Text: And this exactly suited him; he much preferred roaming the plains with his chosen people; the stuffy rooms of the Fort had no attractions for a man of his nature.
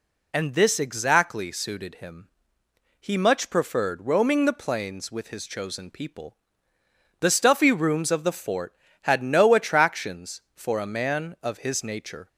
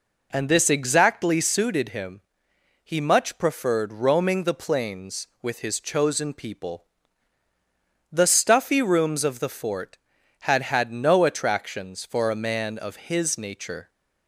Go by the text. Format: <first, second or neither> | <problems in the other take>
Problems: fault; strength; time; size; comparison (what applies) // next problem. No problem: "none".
first | says "had" twice; at 10.6 s